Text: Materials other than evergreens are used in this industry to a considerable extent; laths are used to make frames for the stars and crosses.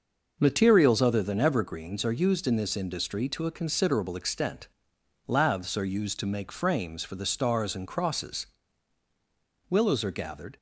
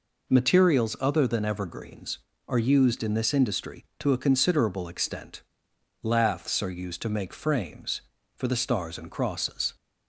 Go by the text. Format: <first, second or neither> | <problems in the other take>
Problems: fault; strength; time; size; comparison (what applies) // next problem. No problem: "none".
second | goes on to say "Willows are gathered"; noticeable; from 9.6 s on; 0.88 s long